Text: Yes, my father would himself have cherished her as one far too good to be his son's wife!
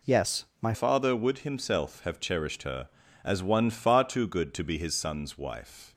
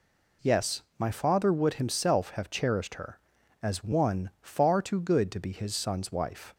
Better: second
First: changes voice at "father"; from 0.7 s on; 5.2 s long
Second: none

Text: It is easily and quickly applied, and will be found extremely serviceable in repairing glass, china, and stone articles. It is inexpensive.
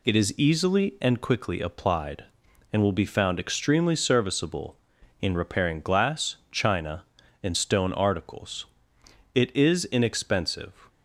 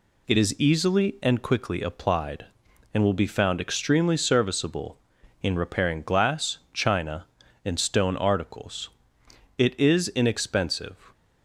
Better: neither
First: none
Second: none

